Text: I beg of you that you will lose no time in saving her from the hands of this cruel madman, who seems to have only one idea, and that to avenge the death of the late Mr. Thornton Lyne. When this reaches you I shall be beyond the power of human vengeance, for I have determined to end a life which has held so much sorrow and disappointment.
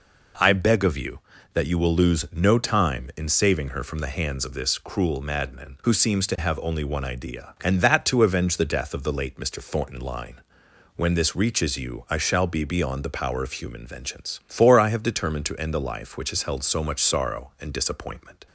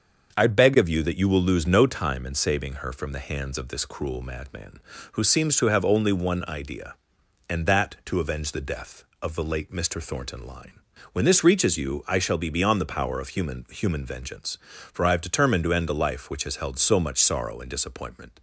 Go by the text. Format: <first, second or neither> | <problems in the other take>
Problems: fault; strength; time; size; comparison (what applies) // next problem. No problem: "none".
first | says "human" twice; at 13.6 s